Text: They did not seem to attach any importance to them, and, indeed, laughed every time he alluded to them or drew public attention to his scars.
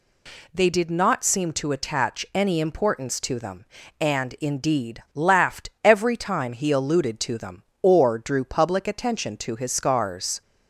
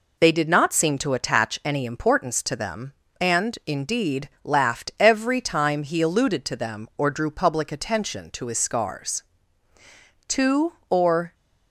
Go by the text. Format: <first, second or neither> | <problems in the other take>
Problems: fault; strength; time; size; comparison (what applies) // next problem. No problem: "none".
first | goes on to say "Two or"; noticeable; from 10.2 s on; 1.0 s long